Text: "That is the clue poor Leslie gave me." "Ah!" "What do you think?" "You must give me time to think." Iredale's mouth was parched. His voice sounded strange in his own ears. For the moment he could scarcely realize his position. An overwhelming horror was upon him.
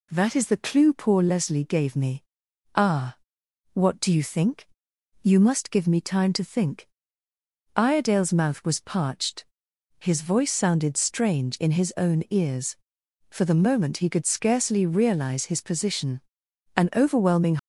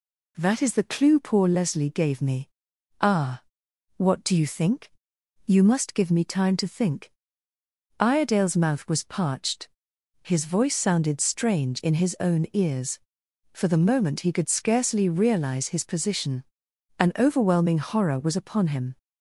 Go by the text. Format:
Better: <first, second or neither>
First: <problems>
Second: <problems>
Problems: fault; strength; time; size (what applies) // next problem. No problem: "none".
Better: second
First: stops before "horror was upon him"; at 17.5 s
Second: none